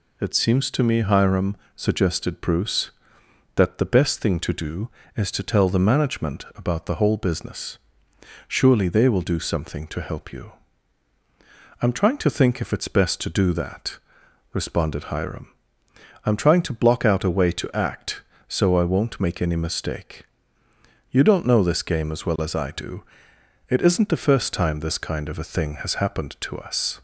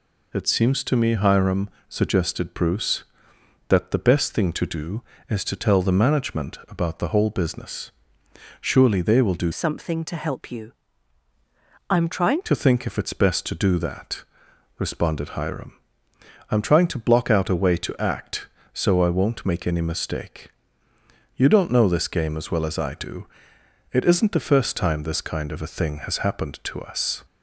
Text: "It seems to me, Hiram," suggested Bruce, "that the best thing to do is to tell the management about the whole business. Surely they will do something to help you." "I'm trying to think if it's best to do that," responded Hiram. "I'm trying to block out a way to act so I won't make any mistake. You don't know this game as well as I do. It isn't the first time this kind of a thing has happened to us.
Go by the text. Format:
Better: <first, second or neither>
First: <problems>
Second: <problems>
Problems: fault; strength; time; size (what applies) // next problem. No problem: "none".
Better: first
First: none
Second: changes voice from "something" to "trying"; from 9.5 to 12.4 s; 2.9 s long